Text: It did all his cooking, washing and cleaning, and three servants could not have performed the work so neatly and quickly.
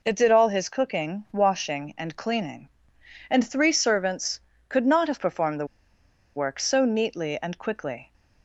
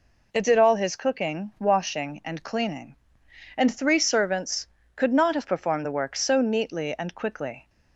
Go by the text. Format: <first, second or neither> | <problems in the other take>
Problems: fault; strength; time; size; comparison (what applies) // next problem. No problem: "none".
second | pauses between "the" and "work"; noticeable; at 5.6 s; 0.70 s long